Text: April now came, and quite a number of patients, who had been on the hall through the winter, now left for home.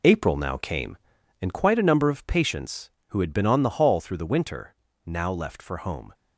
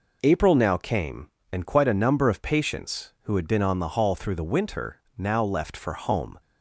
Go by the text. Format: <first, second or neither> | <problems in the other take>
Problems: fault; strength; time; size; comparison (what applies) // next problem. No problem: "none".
second | gets quieter; strong; throughout; 7.5 dB